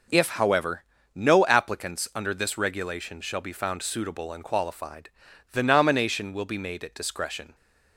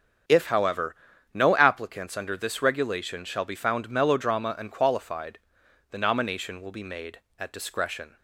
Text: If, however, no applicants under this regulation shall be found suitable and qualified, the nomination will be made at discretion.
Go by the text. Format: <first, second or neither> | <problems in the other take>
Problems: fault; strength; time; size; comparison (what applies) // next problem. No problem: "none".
first | starts louder than the rest; strong; until 1.6 s; 8 dB // says "melodrama" for "suitable"; at 3.8 s